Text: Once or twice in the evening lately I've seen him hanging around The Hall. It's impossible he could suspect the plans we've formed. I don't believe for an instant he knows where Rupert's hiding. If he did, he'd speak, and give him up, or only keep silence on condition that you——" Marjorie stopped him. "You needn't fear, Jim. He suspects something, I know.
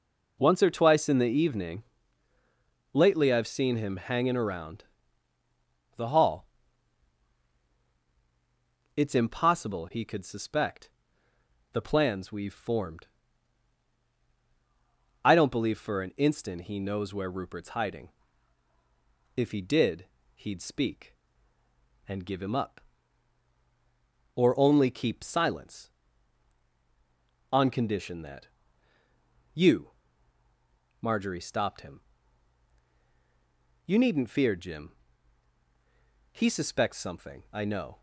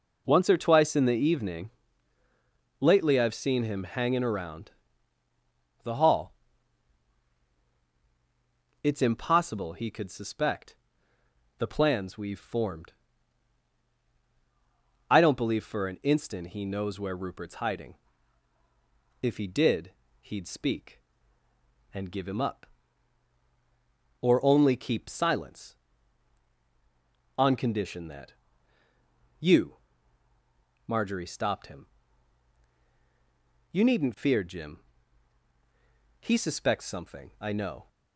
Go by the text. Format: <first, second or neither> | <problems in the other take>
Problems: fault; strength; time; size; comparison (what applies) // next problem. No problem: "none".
neither | pauses between "evening" and "lately"; the same in both // pauses between "around" and "The"; the same in both // pauses between "suspect" and "the"; noticeable; the same in both // pauses between "that" and "you"; the same in both